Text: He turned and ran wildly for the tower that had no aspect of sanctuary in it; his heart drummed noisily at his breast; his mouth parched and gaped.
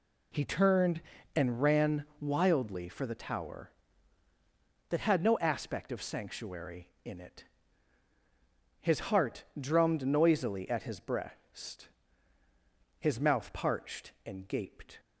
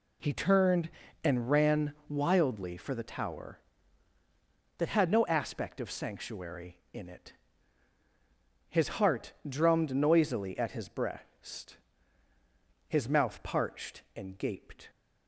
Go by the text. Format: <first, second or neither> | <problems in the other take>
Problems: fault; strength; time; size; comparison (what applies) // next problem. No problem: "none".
neither | pauses between "heart" and "drummed"; slight; the same in both